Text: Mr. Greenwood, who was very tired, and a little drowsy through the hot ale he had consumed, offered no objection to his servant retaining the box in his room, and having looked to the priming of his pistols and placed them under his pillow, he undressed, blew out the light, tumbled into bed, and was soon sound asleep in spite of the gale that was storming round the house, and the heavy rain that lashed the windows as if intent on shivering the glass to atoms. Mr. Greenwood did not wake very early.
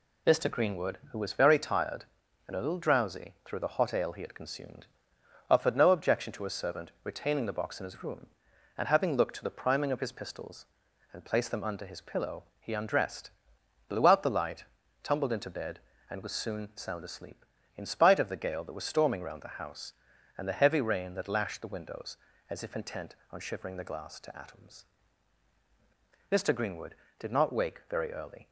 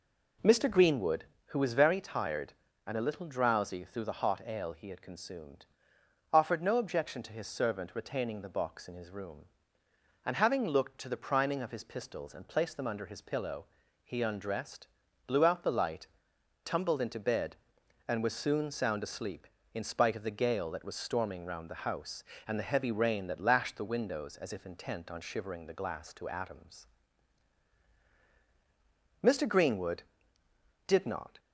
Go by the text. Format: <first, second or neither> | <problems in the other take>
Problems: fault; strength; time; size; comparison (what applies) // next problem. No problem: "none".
first | stops before "wake very early"; at 31.3 s